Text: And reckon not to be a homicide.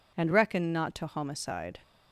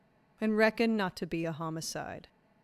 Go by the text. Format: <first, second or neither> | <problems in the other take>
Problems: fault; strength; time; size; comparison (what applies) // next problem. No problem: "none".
second | skips "be a"; at 1.0 s